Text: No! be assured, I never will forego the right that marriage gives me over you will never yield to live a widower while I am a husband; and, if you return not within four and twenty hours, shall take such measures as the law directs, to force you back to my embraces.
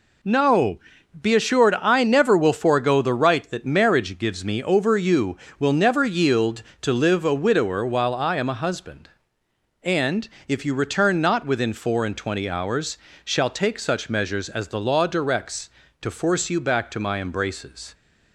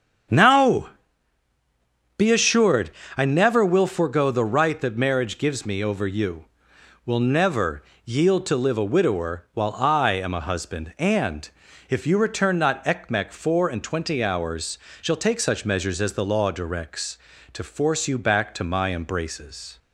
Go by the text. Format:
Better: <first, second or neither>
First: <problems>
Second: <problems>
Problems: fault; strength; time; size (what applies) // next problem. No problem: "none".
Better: first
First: none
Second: starts louder than the rest; strong; until 2.5 s; 7.5 dB // pauses between "never" and "yield"; slight; at 7.8 s; 0.20 s long // says "ekmek" for "within"; at 12.8 s